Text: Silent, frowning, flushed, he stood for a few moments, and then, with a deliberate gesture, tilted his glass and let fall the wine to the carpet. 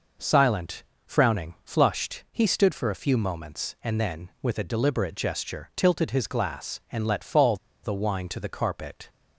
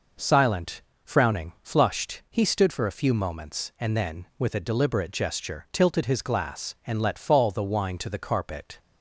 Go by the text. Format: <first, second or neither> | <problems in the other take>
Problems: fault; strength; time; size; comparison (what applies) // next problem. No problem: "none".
second | pauses between "fall" and "the"; slight; at 7.5 s; 0.27 s long